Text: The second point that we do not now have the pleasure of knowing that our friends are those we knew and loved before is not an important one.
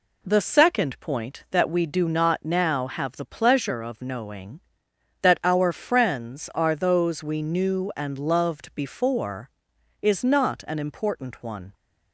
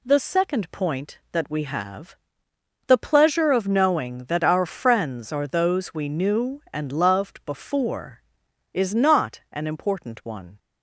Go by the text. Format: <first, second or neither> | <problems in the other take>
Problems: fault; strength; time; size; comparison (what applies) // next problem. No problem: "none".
first | skips "do not now"; at 1.6 s // pauses between "have" and "the"; noticeable; at 2.1 s; 0.72 s long